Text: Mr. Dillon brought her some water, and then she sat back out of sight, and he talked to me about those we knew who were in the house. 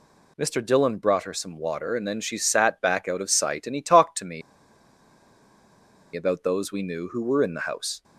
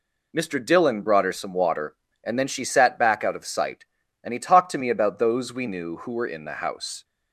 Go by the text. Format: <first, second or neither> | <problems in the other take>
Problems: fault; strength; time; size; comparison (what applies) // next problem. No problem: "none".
second | pauses between "me" and "about"; strong; at 4.4 s; 1.7 s long